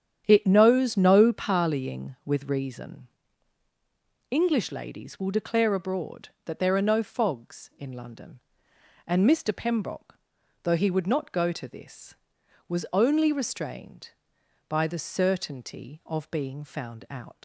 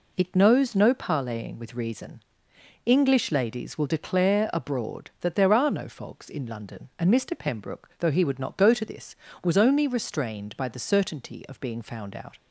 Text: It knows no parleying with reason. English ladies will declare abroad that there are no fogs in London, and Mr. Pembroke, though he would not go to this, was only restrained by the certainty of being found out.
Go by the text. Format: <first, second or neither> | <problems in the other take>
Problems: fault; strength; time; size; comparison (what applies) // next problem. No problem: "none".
second | starts louder than the rest; strong; until 1.2 s; 9 dB // leaves "out" unfinished; at 17.3 s; 85 ms